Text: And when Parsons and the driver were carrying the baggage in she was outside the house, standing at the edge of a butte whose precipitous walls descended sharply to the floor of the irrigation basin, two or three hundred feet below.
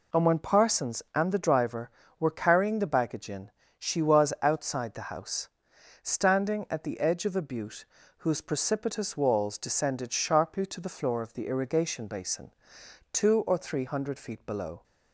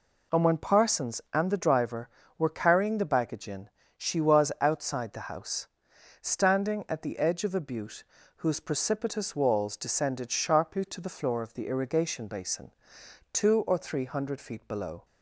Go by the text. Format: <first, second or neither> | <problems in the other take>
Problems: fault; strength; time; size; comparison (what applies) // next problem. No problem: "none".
neither | pauses between "in" and "she"; slight; the same in both // pauses between "butte" and "whose"; slight; the same in both